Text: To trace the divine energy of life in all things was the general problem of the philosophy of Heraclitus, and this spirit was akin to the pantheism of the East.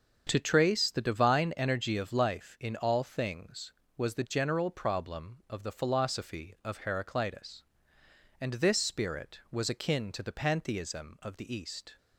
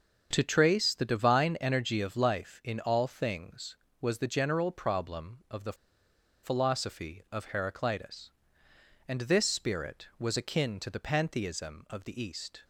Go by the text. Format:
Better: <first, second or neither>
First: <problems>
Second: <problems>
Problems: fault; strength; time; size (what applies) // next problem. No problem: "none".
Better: first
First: starts louder than the rest; until 1.2 s; 7 dB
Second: starts louder than the rest; until 1.3 s; 7 dB // pauses between "the" and "philosophy"; noticeable; at 5.7 s; 0.69 s long